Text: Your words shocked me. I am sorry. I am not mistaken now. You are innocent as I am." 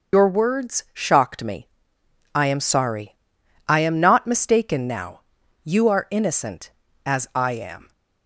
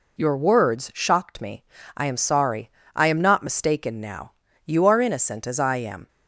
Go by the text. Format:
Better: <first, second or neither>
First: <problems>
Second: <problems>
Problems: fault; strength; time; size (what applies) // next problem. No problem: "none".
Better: second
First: loses the start of "Your"; at 0.1 s; 85 ms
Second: none